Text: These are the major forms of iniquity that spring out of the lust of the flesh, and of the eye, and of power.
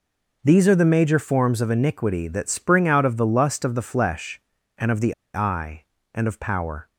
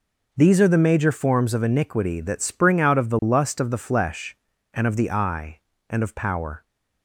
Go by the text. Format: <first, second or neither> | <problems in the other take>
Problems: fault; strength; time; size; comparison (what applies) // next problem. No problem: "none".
second | pauses between "the" and "eye"; slight; at 5.1 s; 0.21 s long